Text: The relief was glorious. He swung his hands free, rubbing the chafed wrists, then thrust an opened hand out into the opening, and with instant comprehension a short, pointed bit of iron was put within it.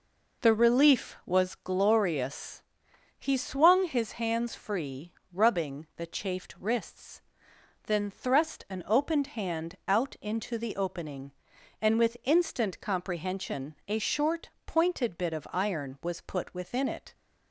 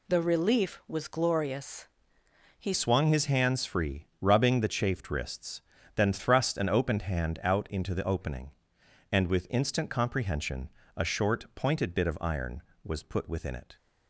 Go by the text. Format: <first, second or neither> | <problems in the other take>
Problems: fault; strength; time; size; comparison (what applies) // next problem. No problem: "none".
first | changes voice at "swung"; from 2.7 s on; 11.0 s long // pauses between "comprehension" and "a"; slight; at 10.6 s; 0.28 s long